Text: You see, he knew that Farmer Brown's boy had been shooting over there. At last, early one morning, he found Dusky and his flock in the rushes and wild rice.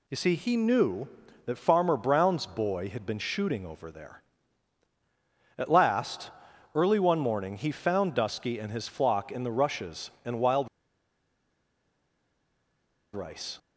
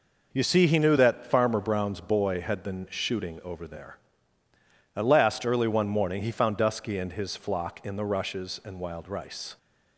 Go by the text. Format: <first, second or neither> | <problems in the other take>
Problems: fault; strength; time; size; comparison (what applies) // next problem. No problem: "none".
second | pauses between "wild" and "rice"; strong; at 10.6 s; 2.4 s long